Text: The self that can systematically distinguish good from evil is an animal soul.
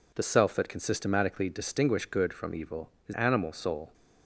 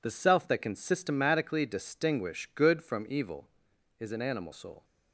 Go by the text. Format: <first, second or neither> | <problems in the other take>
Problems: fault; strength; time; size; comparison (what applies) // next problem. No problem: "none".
second | skips "an"; at 3.1 s